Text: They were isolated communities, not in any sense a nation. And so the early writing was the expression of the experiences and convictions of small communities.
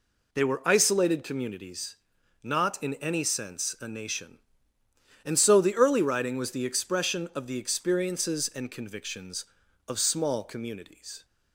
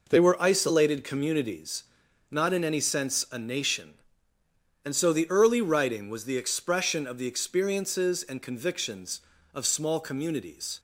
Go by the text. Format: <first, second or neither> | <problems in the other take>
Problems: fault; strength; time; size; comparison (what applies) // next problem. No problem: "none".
neither | none